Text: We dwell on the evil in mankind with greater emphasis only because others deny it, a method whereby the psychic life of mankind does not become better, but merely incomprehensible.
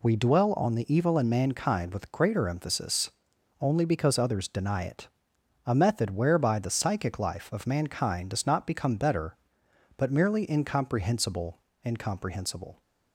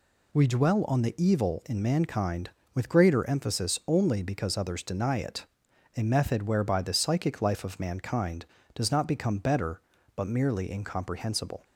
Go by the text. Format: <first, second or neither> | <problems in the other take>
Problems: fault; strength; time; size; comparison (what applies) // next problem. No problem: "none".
second | pauses between "emphasis" and "only"; noticeable; at 3.1 s; 0.52 s long // says "incomprehensible" twice; at 11.8 s